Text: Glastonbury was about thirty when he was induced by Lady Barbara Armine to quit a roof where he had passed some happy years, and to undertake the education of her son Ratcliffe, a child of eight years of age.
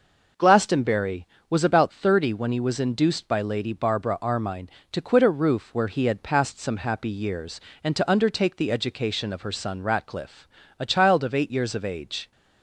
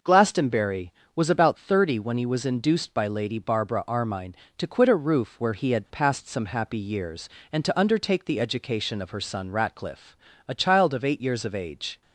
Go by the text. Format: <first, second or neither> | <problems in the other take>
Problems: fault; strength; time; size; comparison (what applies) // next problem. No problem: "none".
neither | none